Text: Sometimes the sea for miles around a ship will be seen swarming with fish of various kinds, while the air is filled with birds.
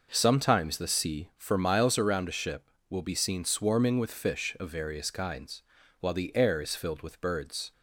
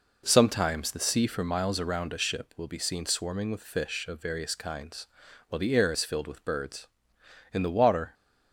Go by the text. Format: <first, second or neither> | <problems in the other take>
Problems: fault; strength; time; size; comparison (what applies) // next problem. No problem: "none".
first | goes on to say "In the water"; noticeable; from 7.5 s on; 0.62 s long